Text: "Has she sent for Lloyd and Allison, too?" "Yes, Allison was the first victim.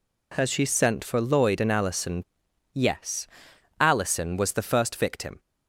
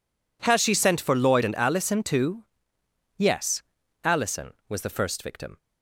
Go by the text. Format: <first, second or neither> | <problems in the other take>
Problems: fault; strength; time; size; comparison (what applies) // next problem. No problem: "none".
second | skips "too"; at 2.4 s